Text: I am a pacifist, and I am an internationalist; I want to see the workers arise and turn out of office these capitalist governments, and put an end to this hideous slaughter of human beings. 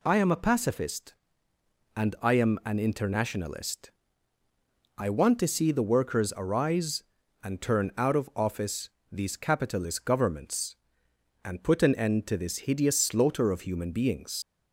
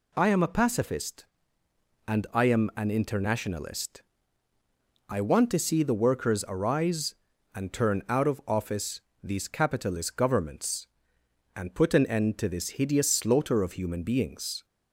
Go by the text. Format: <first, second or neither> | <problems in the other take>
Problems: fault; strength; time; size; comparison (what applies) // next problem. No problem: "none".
second | pauses between "office" and "these"; slight; at 8.8 s; 0.22 s long; slight in the second // leaves "beings" unfinished; at 14.4 s; 110 ms